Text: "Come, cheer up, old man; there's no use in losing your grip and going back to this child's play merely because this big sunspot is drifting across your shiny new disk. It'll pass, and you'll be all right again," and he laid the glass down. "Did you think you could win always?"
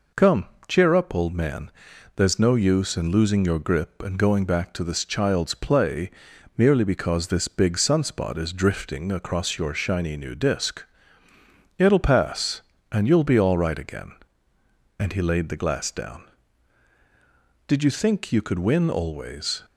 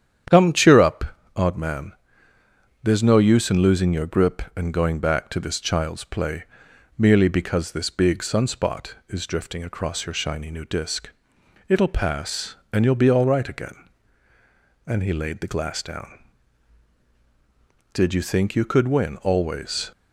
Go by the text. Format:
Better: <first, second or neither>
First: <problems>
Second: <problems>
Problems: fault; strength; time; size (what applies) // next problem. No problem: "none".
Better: first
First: pauses between "play" and "merely"; at 6.1 s; 0.44 s long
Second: starts louder than the rest; strong; until 1.5 s; 9 dB // says "odd" for "old"; at 1.3 s // pauses between "play" and "merely"; noticeable; at 6.4 s; 0.50 s long